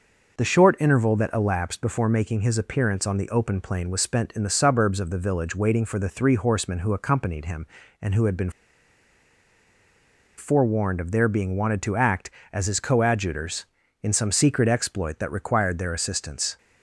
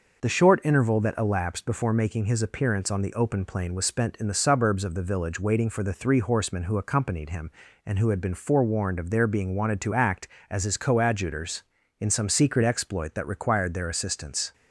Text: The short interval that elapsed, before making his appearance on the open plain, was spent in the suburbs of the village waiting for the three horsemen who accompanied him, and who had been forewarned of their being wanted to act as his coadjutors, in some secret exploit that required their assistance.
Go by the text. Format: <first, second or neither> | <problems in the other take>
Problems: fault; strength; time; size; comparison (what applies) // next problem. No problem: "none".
second | pauses between "been" and "forewarned"; strong; at 8.4 s; 1.8 s long